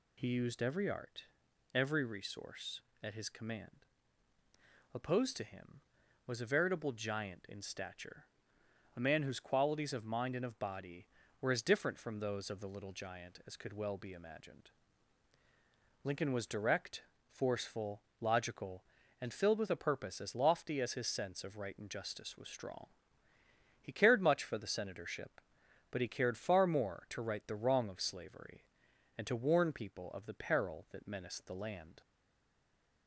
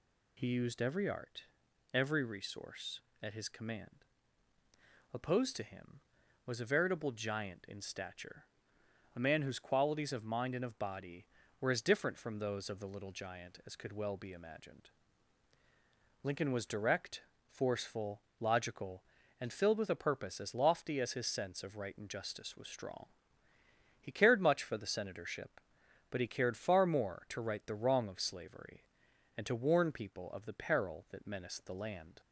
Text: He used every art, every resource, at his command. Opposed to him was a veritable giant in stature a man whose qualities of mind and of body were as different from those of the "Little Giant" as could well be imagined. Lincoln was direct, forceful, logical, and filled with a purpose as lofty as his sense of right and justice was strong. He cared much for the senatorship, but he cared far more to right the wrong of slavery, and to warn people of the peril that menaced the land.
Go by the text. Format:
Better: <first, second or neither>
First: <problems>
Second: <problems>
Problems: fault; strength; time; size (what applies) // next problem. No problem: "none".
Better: second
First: pauses between "stature" and "a"; noticeable; at 8.2 s; 0.72 s long // stays silent after the last word; from 32.0 s on; 1.0 s long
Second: pauses between "stature" and "a"; noticeable; at 8.4 s; 0.72 s long